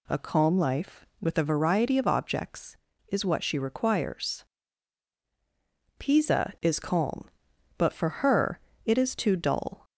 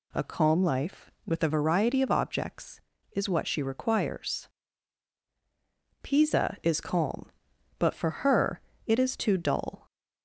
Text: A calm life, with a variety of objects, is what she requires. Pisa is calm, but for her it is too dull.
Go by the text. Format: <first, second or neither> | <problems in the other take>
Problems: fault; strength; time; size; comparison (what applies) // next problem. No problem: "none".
neither | pauses between "her" and "it"; slight; the same in both